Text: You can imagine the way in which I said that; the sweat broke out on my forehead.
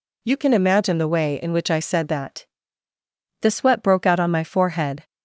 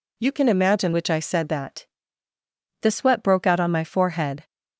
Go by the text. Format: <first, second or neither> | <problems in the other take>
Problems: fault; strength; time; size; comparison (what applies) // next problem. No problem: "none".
first | skips "the way in"; at 0.9 s